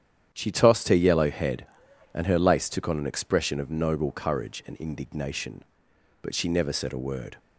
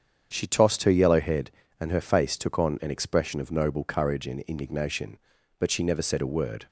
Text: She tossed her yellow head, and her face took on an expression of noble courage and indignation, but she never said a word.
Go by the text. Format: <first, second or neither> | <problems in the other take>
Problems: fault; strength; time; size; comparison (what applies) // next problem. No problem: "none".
second | starts louder than the rest; strong; until 1.3 s; 9.5 dB; strong in the second // says "lace" for "face"; at 2.3 s